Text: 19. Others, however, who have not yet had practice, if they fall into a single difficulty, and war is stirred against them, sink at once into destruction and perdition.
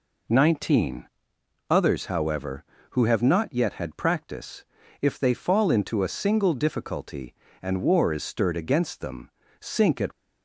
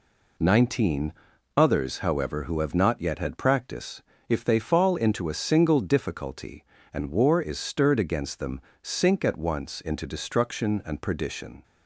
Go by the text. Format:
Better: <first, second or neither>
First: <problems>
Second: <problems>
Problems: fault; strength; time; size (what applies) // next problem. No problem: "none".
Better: second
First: stops before "once into destruction and perdition"; at 10.1 s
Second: none